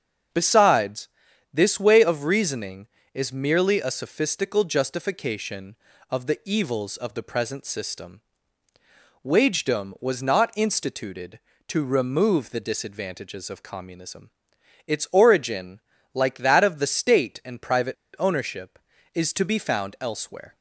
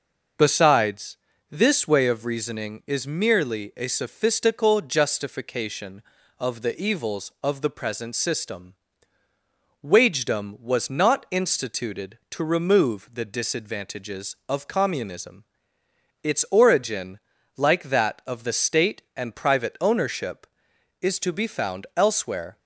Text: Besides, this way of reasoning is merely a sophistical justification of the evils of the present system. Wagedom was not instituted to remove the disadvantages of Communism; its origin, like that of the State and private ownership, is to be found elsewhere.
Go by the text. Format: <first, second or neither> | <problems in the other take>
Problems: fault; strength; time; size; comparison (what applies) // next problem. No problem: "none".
second | starts louder than the rest; until 1.7 s; 7 dB // pauses between "private" and "ownership"; slight; at 17.9 s; 0.23 s long